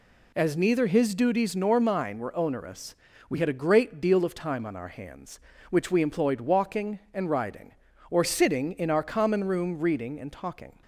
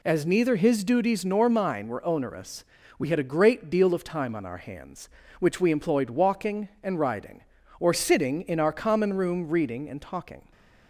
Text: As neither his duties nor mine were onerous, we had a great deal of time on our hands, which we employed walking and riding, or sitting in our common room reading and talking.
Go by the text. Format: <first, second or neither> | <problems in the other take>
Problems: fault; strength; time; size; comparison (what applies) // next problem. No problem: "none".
neither | none